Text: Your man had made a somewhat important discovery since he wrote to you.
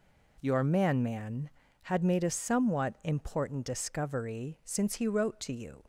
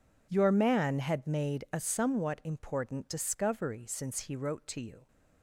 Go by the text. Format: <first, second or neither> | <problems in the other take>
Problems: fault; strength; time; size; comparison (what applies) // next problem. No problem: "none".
second | says "man" twice; at 1.0 s